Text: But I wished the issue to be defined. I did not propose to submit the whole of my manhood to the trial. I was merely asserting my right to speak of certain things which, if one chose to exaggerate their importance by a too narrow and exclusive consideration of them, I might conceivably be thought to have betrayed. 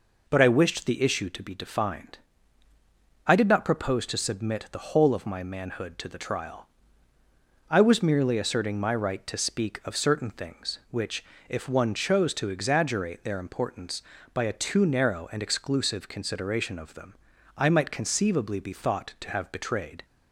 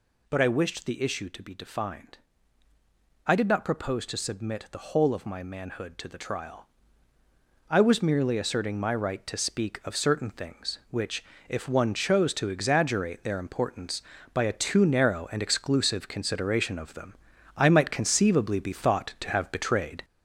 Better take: first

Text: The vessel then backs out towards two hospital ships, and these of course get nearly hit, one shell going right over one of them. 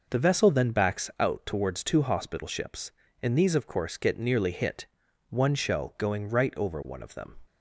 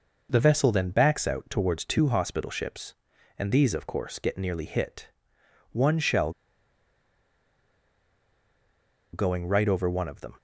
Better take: first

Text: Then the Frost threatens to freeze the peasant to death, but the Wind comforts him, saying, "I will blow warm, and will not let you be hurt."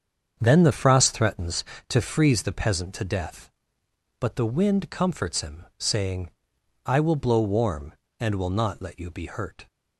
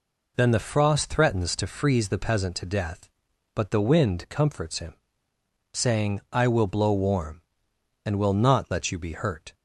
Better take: second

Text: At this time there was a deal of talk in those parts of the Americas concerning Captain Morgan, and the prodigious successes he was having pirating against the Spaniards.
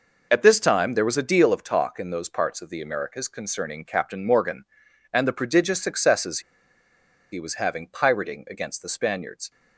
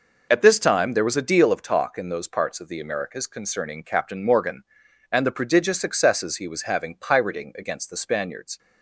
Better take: second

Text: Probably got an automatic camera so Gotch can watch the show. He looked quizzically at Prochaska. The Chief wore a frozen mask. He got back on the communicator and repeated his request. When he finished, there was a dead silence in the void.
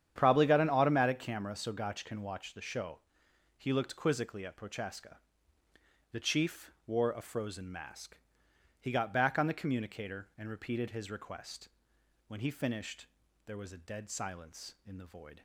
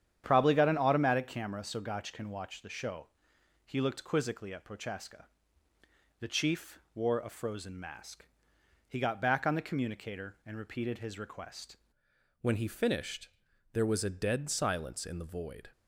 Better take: first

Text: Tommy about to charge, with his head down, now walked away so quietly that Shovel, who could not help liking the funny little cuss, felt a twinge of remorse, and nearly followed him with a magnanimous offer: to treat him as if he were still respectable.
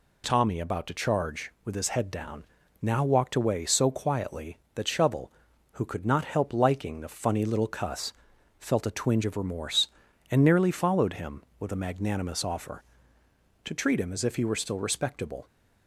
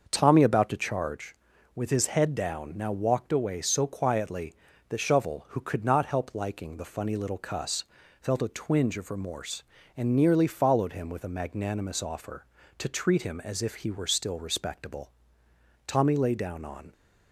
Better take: first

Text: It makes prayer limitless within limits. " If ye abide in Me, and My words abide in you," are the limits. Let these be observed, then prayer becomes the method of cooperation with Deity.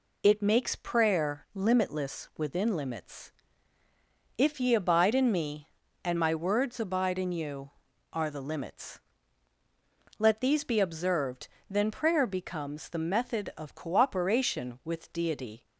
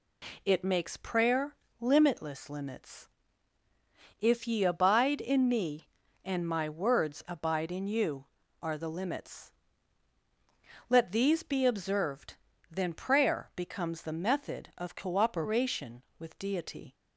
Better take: first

